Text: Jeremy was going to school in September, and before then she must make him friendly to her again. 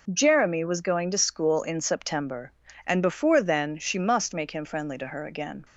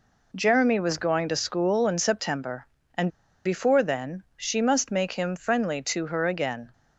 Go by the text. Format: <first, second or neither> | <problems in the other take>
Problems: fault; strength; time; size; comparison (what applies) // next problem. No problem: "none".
first | pauses between "and" and "before"; slight; at 3.0 s; 0.35 s long